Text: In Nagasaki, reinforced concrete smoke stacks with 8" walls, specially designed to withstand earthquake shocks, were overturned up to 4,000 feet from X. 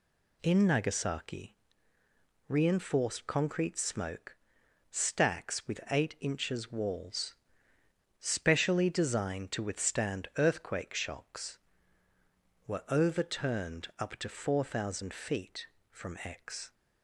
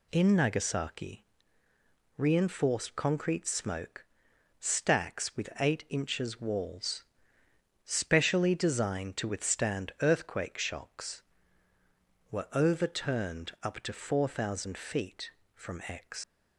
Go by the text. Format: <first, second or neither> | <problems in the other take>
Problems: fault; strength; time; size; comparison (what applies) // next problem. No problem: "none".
first | pauses between "smoke" and "stacks"; noticeable; at 4.0 s; 0.52 s long; noticeable in the first // leaves "X" unfinished; at 16.2 s; 135 ms